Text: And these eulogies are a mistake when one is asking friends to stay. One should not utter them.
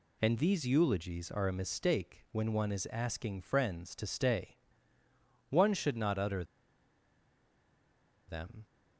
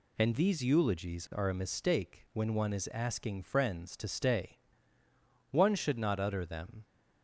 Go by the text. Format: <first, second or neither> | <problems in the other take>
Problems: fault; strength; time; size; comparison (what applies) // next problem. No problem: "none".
second | pauses between "utter" and "them"; strong; at 6.4 s; 1.8 s long